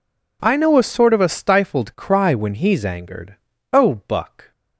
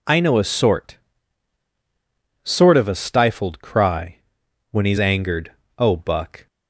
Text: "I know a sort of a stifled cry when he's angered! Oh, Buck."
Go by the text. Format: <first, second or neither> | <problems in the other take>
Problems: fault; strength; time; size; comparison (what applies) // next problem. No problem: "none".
first | says "sort" twice; at 2.4 s // pauses between "cry" and "when"; noticeable; at 4.1 s; 0.52 s long